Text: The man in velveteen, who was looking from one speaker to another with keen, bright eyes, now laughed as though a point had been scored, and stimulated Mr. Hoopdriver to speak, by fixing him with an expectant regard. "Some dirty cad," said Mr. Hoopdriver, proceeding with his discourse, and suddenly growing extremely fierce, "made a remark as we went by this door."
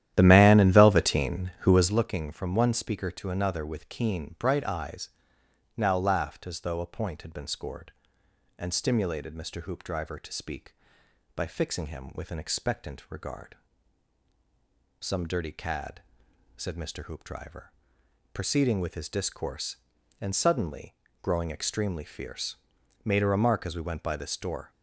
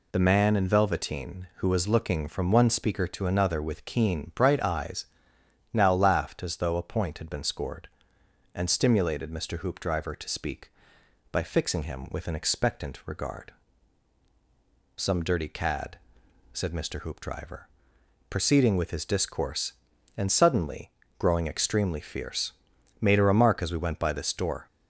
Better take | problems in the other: second | starts louder than the rest; strong; until 2.1 s; 12 dB // pauses between "suddenly" and "growing"; slight; at 20.9 s; 0.28 s long; slight in the second

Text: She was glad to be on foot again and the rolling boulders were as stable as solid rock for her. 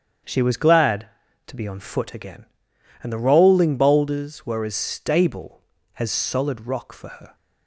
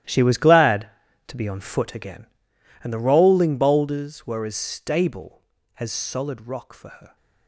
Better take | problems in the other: first | gets quieter; strong; throughout; 15.5 dB // starts louder than the rest; strong; until 1.4 s; 13 dB; strong in the first

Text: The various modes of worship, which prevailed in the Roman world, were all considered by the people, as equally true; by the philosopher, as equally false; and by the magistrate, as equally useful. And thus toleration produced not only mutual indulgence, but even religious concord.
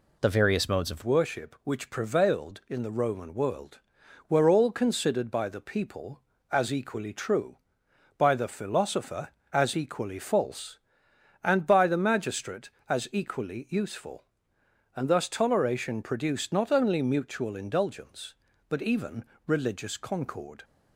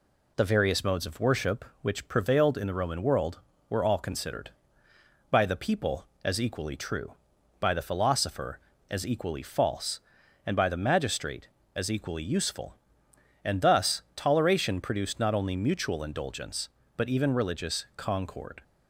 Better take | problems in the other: second | changes voice at "worship"; from 1.0 s on; 19.6 s long // pauses between "even" and "religious"; slight; at 19.2 s; 0.22 s long

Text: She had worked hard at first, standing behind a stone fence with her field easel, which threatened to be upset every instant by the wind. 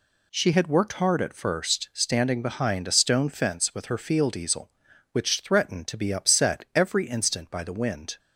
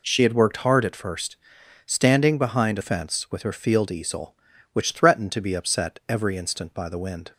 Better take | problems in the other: first | skips "stone"; at 2.8 s

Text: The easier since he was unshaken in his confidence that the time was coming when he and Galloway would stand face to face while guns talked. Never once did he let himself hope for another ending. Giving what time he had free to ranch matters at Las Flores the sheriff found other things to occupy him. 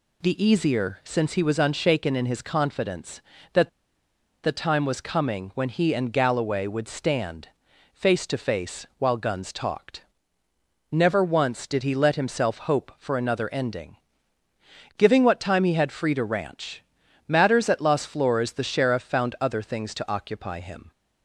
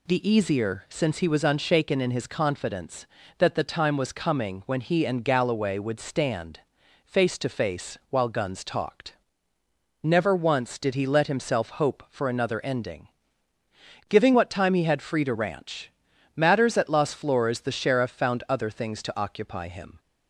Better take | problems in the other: second | pauses between "that" and "the"; noticeable; at 3.6 s; 0.74 s long // pauses between "stand" and "face"; at 7.4 s; 0.44 s long; also in the second // pauses between "ranch" and "matters"; at 16.8 s; 0.44 s long; also in the second

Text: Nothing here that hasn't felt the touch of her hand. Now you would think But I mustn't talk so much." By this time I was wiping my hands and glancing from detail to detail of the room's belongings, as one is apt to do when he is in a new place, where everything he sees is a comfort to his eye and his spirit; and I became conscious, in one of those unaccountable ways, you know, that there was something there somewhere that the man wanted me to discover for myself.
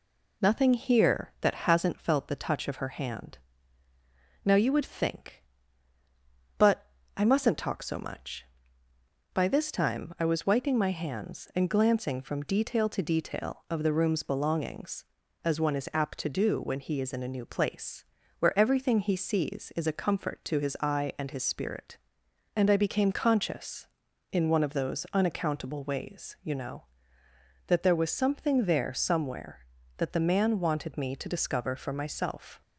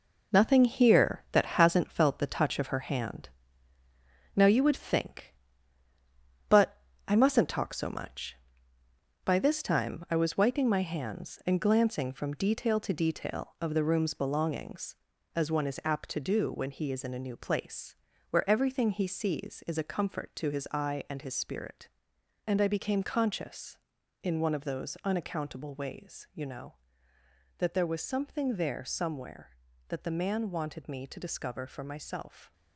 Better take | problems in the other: first | gets quieter; strong; throughout; 8 dB // pauses between "But" and "I"; slight; at 6.7 s; 0.32 s long; slight in the first

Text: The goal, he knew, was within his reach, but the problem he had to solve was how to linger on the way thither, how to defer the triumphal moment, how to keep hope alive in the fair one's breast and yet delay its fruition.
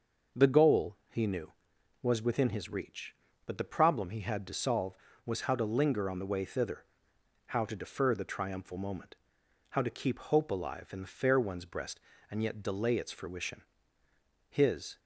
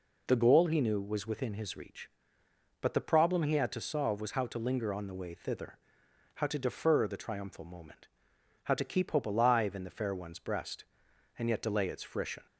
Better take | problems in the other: second | goes on to say "His"; from 14.4 s on; 0.50 s long

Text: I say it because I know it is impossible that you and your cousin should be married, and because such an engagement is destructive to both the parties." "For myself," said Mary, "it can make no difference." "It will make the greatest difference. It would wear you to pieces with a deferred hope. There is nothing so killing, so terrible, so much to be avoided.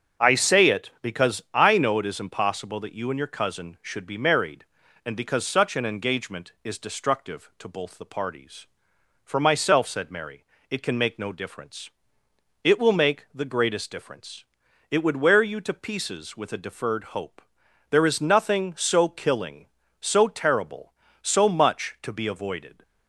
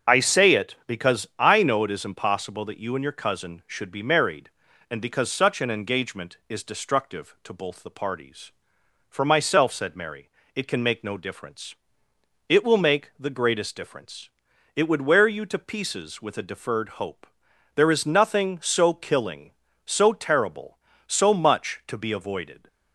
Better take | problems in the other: first | loses the start of "I"; at 0.0 s; 20 ms // starts louder than the rest; until 1.1 s; 7 dB; strong in the first

